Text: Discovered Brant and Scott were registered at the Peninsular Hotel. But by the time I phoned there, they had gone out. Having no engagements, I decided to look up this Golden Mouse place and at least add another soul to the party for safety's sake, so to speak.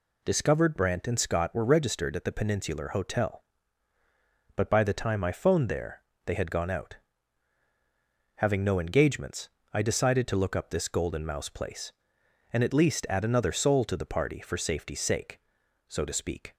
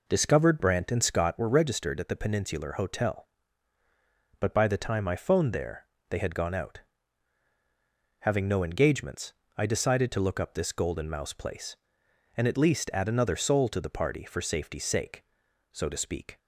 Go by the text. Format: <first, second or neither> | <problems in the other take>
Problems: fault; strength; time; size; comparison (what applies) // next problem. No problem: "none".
first | starts louder than the rest; noticeable; until 1.5 s; 4.5 dB